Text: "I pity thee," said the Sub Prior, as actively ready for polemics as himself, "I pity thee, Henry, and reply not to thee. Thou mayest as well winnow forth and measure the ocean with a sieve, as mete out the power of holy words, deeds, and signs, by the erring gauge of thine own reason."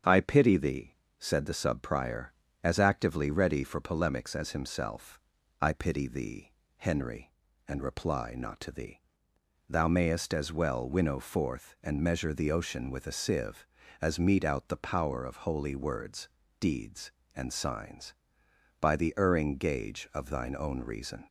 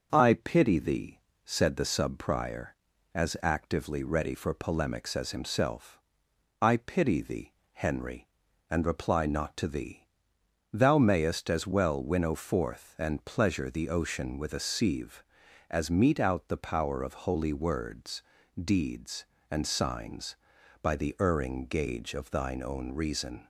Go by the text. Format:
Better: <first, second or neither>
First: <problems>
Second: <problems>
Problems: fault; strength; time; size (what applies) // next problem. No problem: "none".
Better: first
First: starts louder than the rest; strong; until 1.2 s; 7.5 dB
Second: starts louder than the rest; until 1.1 s; 6.5 dB // says "pleasure" for "measure"; at 13.2 s